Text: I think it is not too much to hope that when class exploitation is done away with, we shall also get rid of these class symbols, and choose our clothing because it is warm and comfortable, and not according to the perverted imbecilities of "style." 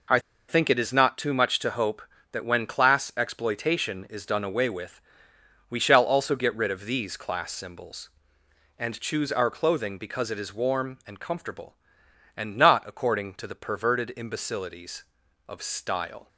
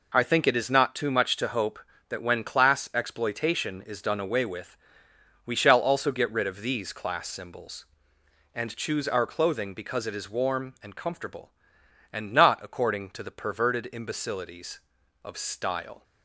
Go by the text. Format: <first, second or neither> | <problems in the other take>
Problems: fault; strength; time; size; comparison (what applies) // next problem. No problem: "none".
second | pauses between "I" and "think"; slight; at 0.1 s; 0.29 s long